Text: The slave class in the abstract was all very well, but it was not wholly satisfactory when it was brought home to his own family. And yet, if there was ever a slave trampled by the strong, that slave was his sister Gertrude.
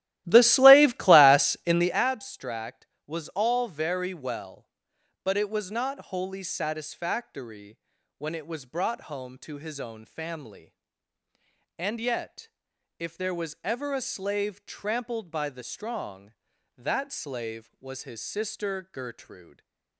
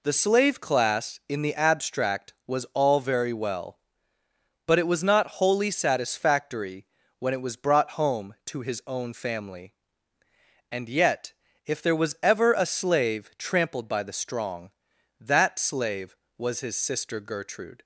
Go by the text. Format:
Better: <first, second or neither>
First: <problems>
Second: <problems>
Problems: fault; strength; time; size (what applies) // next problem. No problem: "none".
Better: second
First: starts louder than the rest; strong; until 2.1 s; 15 dB // pauses between "satisfactory" and "when"; at 7.7 s; 0.40 s long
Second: pauses between "satisfactory" and "when"; slight; at 6.8 s; 0.34 s long